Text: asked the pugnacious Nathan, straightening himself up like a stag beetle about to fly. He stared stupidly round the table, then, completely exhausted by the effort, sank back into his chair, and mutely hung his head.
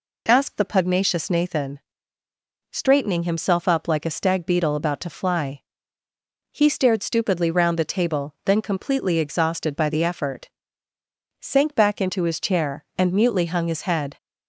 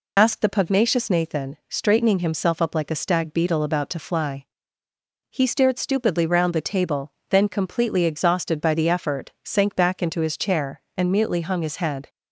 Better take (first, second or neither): first